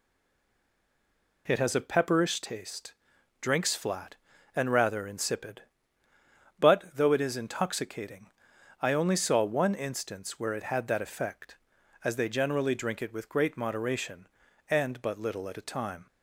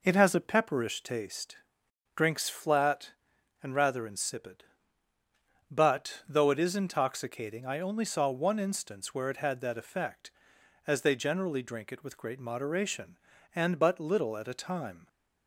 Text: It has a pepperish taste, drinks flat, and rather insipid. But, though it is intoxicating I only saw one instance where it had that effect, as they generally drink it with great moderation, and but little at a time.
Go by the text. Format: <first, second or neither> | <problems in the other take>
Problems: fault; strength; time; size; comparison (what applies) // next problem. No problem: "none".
second | stays silent before the first word; noticeable; until 1.4 s; 1.4 s long // pauses between "intoxicating" and "I"; noticeable; at 8.2 s; 0.56 s long